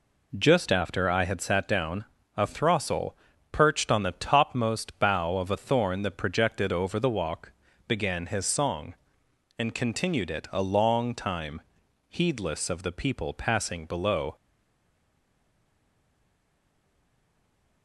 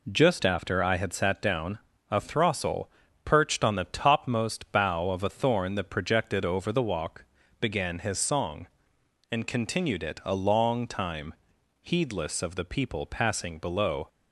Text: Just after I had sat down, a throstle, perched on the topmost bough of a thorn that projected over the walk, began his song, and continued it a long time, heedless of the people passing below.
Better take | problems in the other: second | stays silent after the last word; strong; from 14.3 s on; 3.5 s long

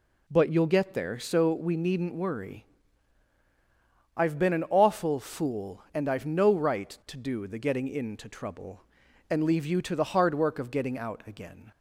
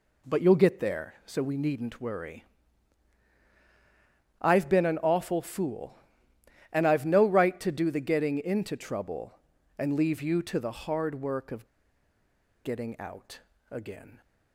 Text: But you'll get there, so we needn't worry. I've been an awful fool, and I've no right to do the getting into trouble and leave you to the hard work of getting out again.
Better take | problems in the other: first | pauses between "of" and "getting"; at 11.6 s; 0.98 s long // pauses between "out" and "again"; slight; at 13.3 s; 0.32 s long

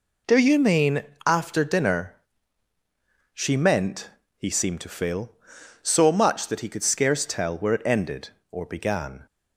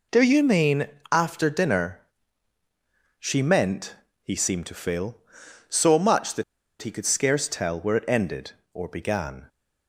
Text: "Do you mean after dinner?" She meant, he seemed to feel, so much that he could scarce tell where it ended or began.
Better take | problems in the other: first | pauses between "mean" and "after"; slight; at 0.8 s; 0.24 s long; slight in the first // pauses between "that" and "he"; at 6.4 s; 0.38 s long

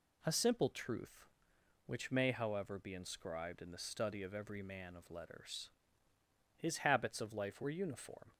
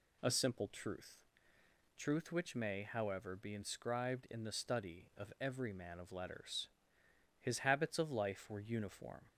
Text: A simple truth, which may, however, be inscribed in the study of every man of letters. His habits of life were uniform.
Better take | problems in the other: first | says "truth" twice; at 1.9 s

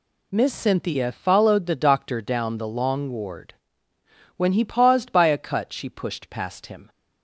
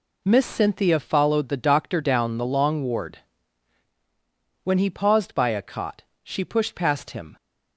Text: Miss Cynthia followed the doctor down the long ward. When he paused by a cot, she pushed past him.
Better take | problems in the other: second | says "cut" for "cot"; at 5.3 s

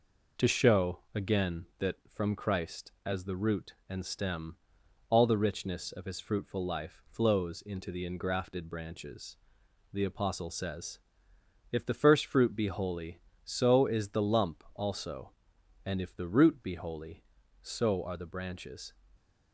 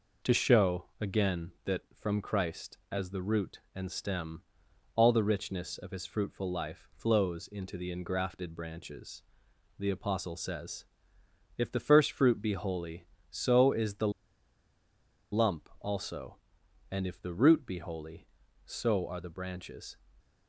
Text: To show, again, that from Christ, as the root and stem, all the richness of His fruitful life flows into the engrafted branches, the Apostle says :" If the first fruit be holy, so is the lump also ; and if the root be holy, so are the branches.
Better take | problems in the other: first | pauses between "the" and "lump"; at 14.0 s; 1.2 s long

